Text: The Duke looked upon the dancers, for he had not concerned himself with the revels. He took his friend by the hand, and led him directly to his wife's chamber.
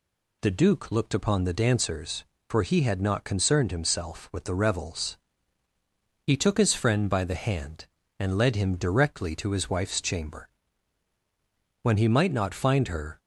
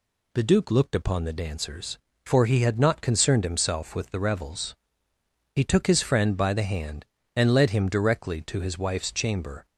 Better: second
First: goes on to say "When he might not find her"; from 11.8 s on; 1.3 s long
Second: none

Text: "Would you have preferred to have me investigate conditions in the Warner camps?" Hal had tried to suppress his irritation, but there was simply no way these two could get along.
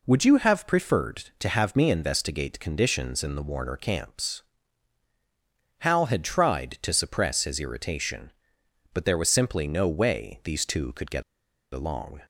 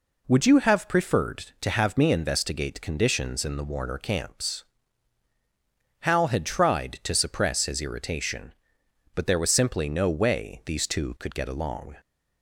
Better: second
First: pauses between "get" and "along"; noticeable; at 11.2 s; 0.49 s long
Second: none

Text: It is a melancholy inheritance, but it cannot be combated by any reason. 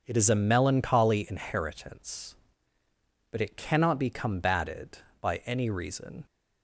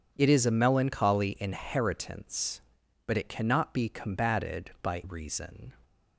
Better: first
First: none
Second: skips "any"; at 5.0 s

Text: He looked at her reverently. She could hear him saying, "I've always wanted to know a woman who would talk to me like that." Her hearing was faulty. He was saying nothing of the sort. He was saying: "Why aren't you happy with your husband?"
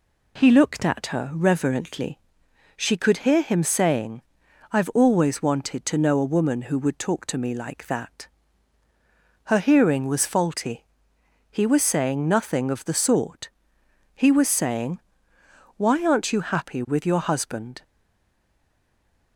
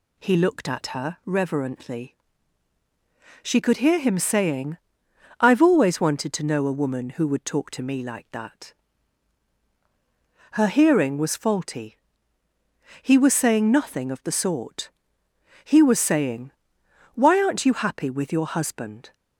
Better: second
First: stays silent after the last word; noticeable; from 17.8 s on; 1.5 s long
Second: none

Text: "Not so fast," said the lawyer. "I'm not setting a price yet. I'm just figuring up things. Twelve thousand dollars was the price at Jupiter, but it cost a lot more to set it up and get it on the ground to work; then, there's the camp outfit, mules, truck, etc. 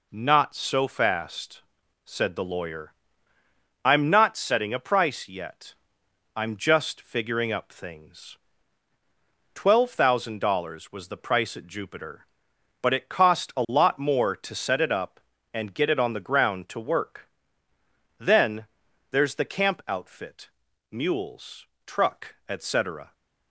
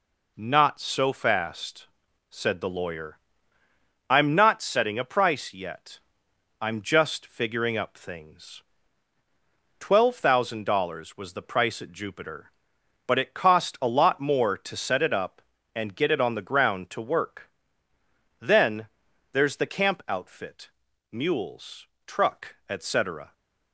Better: neither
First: none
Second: none

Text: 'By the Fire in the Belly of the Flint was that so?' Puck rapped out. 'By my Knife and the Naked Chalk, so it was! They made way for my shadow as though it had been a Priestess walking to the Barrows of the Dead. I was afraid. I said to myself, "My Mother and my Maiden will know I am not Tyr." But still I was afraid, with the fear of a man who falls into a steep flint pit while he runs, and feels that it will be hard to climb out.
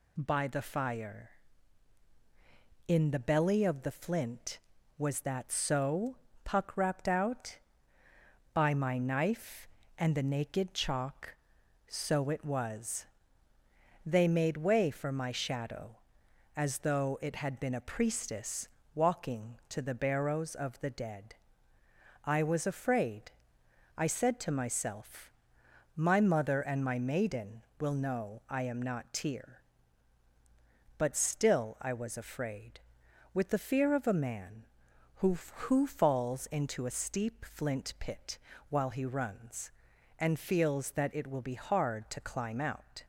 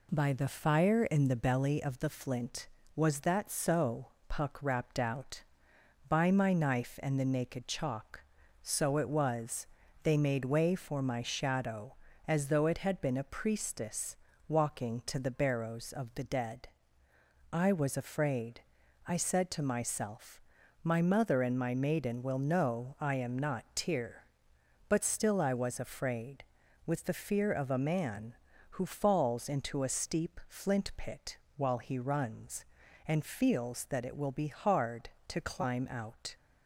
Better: second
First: pauses between "Priestess" and "walking"; slight; at 18.6 s; 0.26 s long // says "who" twice; at 35.3 s // pauses between "pit" and "while"; slight; at 38.3 s; 0.32 s long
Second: pauses between "Priestess" and "walking"; slight; at 14.1 s; 0.32 s long // pauses between "pit" and "while"; slight; at 31.3 s; 0.18 s long

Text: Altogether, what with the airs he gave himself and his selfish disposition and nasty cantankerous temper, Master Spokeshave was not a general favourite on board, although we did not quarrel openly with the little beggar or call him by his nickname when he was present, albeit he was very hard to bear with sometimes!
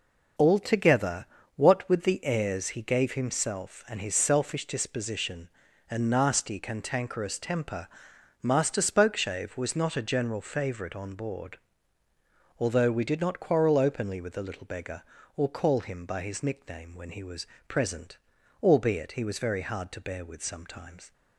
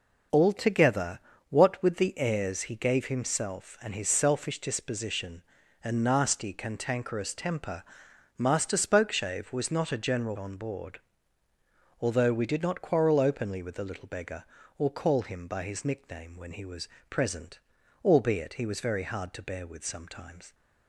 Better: first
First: pauses between "was" and "present"; slight; at 17.4 s; 0.22 s long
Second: skips "favourite"; at 10.3 s // pauses between "was" and "present"; slight; at 16.8 s; 0.22 s long

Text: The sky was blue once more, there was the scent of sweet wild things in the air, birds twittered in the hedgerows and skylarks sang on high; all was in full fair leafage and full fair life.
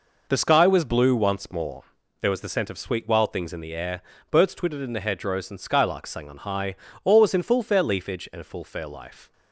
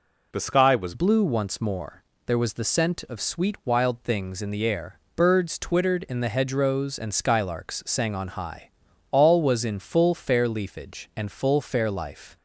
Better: first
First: none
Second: changes voice at "blue"; from 0.9 s on; 11.4 s long

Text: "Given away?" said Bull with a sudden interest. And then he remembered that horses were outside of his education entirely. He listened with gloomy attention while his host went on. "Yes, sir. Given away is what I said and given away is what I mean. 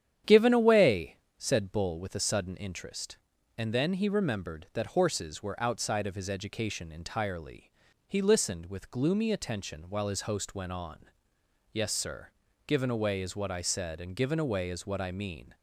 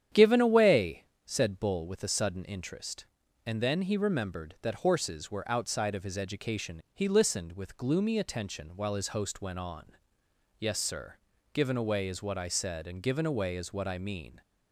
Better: first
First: starts louder than the rest; strong; until 1.4 s; 9.5 dB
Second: starts louder than the rest; strong; until 1.3 s; 9.5 dB // skips "entirely"; at 6.8 s

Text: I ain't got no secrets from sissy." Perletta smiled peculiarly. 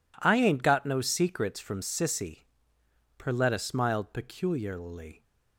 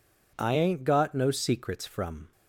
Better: first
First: none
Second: stops before "sissy Perletta smiled peculiarly"; at 2.3 s

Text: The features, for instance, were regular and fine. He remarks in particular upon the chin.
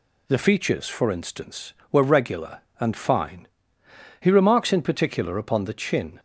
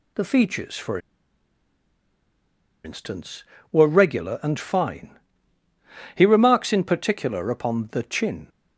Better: first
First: none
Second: pauses between "for" and "instance"; strong; at 0.9 s; 1.8 s long

